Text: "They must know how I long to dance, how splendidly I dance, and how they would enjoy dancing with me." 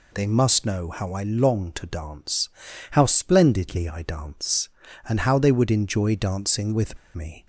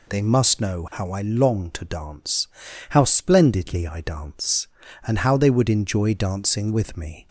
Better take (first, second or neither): second